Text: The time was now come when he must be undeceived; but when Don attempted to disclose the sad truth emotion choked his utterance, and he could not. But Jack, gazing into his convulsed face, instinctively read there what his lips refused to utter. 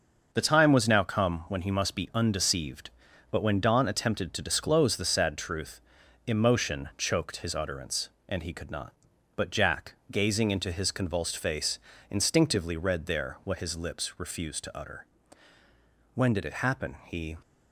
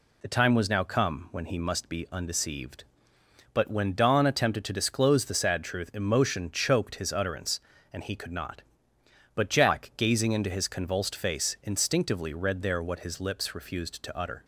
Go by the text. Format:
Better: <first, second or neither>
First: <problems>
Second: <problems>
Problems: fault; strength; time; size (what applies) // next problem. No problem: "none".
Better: second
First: starts louder than the rest; until 1.3 s; 6.5 dB // pauses between "truth" and "emotion"; noticeable; at 5.7 s; 0.46 s long // goes on to say "When did it happen he"; noticeable; from 16.1 s on; 1.2 s long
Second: none